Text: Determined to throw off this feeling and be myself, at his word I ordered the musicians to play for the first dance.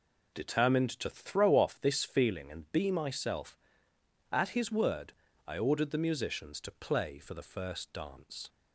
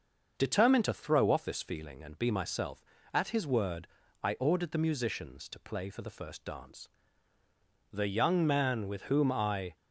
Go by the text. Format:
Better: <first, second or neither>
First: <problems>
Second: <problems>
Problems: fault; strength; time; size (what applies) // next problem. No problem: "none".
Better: first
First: pauses between "word" and "I"; slight; at 5.1 s; 0.34 s long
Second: starts louder than the rest; until 1.3 s; 6.5 dB // pauses between "word" and "I"; slight; at 3.8 s; 0.34 s long // goes on to say "The young man with whom I"; strong; from 7.8 s on; 1.8 s long